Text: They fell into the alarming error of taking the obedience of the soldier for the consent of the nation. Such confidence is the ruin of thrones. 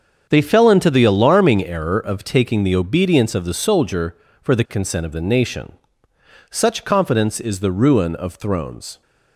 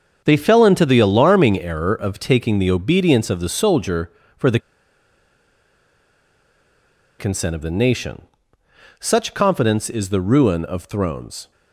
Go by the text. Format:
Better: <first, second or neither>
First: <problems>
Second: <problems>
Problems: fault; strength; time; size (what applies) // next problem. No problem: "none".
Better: first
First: starts louder than the rest; strong; until 1.3 s; 7 dB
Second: starts louder than the rest; strong; until 1.2 s; 7 dB // pauses between "the" and "consent"; strong; at 4.5 s; 2.6 s long